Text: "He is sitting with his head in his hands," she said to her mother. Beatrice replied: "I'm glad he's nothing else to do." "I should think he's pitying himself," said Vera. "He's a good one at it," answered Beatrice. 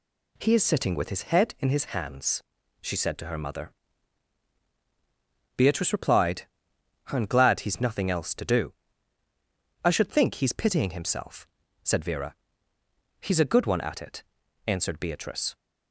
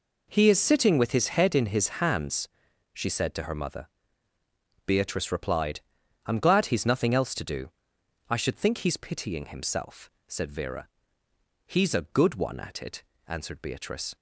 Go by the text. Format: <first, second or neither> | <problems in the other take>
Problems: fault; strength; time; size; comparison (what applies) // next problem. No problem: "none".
neither | none